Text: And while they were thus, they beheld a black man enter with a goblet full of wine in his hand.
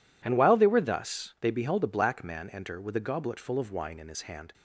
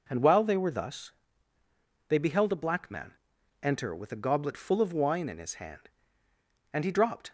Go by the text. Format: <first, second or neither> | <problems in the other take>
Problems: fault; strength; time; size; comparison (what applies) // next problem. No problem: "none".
first | pauses between "man" and "enter"; noticeable; at 3.1 s; 0.48 s long // goes on to say "And he dropped"; from 6.7 s on; 0.58 s long